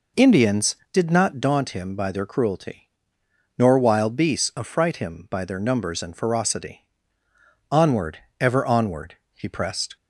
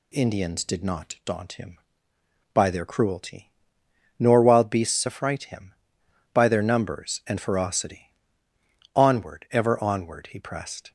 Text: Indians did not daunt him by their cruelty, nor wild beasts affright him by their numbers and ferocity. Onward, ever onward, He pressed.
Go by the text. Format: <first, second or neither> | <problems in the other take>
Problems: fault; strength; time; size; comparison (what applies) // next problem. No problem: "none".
neither | none